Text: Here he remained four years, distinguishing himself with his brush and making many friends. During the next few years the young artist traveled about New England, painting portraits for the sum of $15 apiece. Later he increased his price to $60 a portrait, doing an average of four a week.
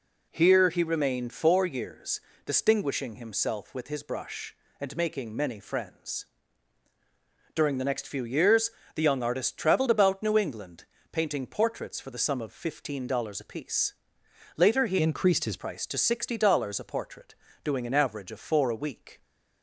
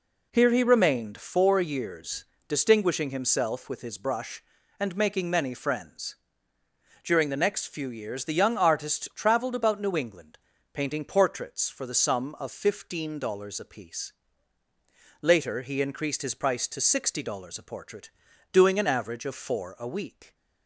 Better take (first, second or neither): second